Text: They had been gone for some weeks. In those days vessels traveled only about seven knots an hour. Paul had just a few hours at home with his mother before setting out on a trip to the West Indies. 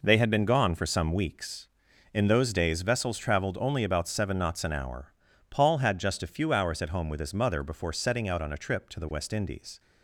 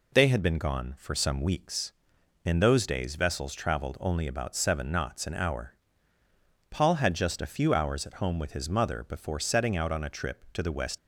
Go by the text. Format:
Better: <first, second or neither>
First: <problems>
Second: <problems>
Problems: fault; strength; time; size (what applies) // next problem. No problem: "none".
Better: first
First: none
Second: stops before "Indies"; at 10.9 s